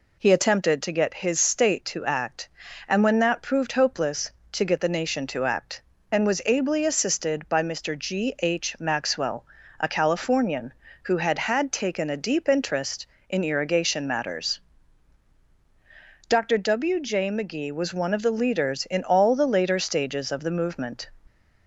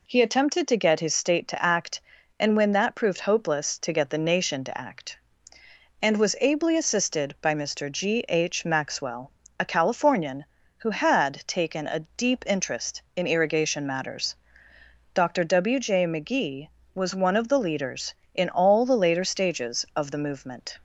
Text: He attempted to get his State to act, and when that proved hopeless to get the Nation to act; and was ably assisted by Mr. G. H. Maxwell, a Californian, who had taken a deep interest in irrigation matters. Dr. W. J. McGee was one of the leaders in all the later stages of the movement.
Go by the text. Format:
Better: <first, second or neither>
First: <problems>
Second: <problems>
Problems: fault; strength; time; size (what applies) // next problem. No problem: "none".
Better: second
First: says "had" twice; at 11.3 s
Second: none